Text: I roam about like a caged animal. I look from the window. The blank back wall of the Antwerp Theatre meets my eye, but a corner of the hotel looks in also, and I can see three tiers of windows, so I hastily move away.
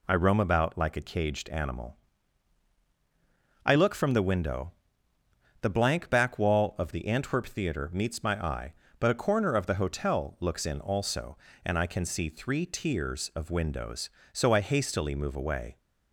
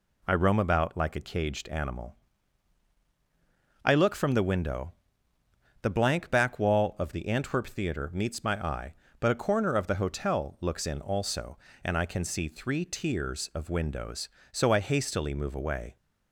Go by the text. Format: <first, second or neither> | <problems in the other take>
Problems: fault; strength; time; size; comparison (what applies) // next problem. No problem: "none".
neither | none